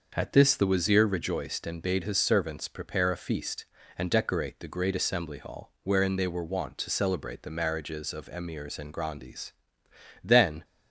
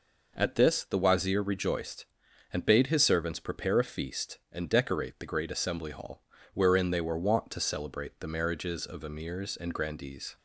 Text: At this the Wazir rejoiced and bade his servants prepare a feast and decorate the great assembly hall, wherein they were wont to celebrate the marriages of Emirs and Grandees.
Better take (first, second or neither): second